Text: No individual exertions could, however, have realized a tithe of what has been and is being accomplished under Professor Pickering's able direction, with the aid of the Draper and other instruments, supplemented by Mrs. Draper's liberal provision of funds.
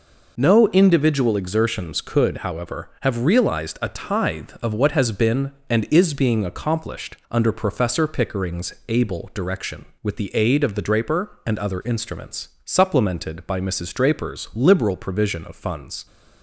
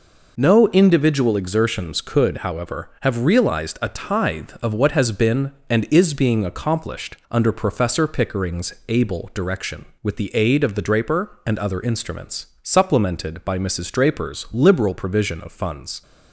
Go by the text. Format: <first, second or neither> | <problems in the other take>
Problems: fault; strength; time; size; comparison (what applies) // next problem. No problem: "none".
neither | none